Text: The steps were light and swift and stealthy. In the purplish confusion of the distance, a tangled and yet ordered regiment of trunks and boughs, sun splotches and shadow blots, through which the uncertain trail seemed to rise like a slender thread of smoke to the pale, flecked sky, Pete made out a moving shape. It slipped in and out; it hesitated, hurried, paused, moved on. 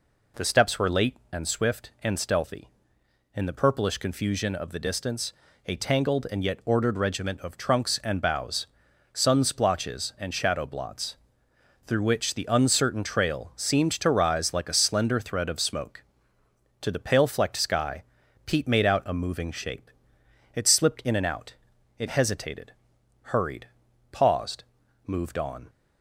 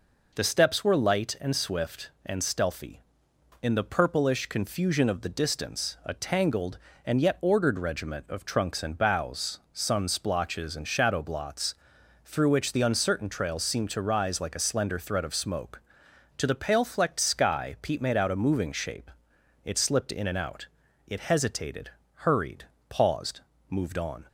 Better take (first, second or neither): second